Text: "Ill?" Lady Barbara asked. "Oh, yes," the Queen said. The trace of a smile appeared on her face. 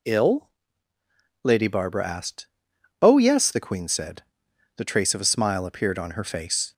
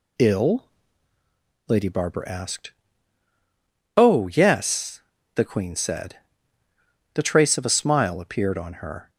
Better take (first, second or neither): first